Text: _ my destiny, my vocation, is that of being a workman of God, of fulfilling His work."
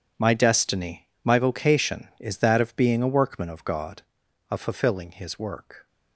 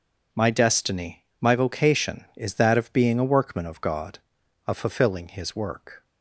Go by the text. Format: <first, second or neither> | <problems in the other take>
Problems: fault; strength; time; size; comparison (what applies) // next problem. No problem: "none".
second | gets quieter; strong; throughout; 14.5 dB